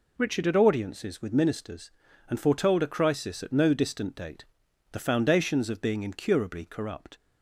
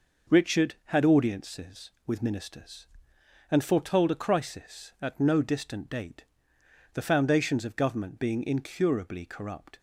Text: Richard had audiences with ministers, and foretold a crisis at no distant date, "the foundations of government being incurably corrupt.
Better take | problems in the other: second | skips "government"; at 5.8 s

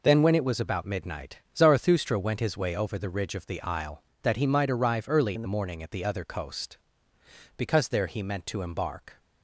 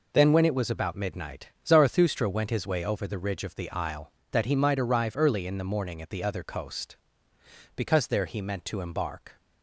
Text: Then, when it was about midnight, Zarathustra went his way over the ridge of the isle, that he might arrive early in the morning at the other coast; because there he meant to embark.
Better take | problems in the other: second | changes voice from "in" to "the"; from 5.3 to 5.4 s; 0.1 s long

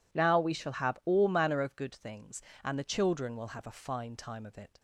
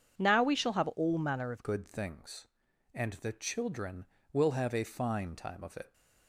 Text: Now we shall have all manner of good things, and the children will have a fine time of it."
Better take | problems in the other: first | changes voice at "good"; from 1.6 s on; 4.3 s long

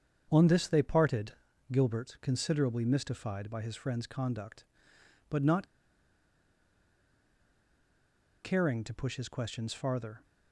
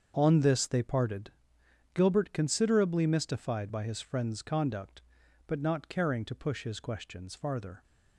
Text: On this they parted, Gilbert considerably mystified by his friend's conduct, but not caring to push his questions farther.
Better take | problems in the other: second | starts louder than the rest; strong; until 1.3 s; 7.5 dB; also in the second // pauses between "not" and "caring"; strong; at 5.6 s; 2.7 s long

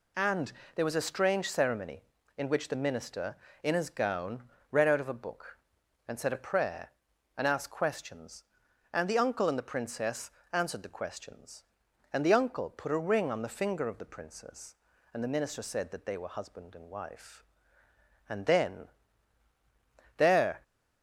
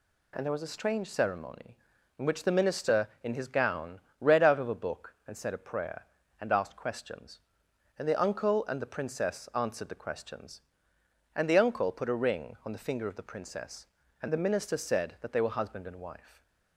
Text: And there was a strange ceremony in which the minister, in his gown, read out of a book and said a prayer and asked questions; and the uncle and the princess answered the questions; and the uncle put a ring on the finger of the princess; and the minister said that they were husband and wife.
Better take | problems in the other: second | pauses between "And" and "there"; slight; at 0.5 s; 0.24 s long // pauses between "princess" and "answered"; slight; at 10.3 s; 0.22 s long // goes on to say "And then there"; strong; from 18.2 s on; 2.3 s long

